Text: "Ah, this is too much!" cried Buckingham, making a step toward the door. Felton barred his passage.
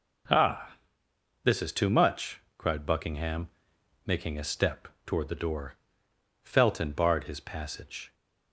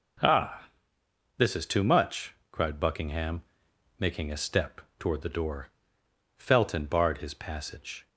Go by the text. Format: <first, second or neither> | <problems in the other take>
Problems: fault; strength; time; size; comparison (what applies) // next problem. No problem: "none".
neither | pauses between "step" and "toward"; slight; the same in both